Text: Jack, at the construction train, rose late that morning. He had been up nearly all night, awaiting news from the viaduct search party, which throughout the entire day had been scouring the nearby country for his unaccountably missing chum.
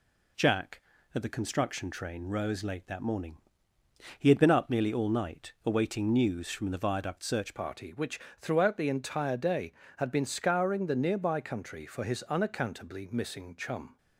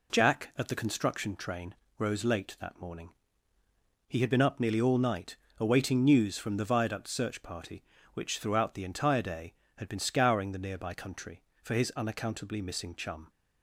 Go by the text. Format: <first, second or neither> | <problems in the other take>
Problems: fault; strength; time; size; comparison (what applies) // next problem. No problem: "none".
second | changes voice at "party"; from 7.5 s on; 6.4 s long // pauses between "which" and "throughout"; slight; at 8.1 s; 0.18 s long